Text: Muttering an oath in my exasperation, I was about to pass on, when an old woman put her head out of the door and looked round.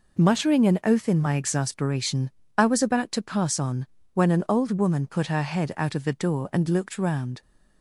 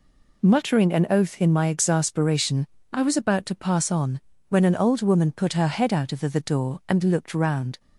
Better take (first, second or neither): first